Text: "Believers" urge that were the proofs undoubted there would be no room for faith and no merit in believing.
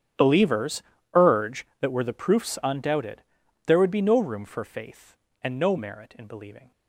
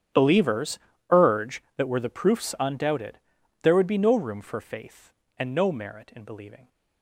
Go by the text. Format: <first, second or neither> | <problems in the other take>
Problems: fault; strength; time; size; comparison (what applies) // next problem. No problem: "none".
neither | starts louder than the rest; strong; the same in both // pauses between "Believers" and "urge"; slight; the same in both // pauses between "undoubted" and "there"; the same in both